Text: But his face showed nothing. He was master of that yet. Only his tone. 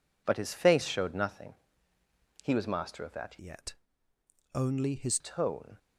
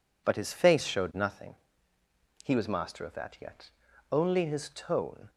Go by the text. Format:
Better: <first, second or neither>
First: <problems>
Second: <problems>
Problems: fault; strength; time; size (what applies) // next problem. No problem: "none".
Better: second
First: changes voice from "yet" to "his"; from 3.3 to 5.1 s; 1.8 s long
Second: none